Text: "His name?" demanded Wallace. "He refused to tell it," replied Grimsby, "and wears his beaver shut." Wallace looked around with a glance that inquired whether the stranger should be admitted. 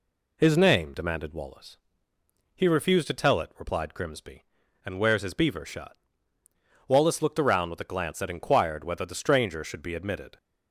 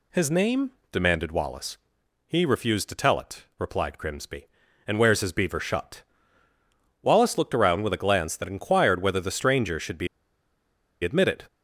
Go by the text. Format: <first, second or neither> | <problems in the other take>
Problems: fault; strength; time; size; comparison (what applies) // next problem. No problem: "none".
first | pauses between "be" and "admitted"; noticeable; at 10.0 s; 0.96 s long